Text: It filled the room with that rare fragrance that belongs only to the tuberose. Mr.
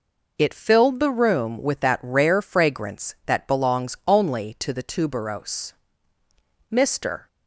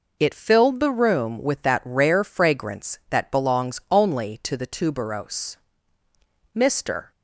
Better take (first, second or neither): neither